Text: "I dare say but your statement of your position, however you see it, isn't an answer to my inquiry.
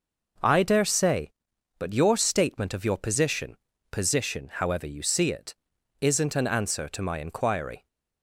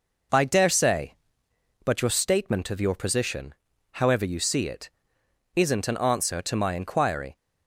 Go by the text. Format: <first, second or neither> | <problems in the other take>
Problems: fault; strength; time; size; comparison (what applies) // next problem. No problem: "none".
second | says "position" twice; at 3.9 s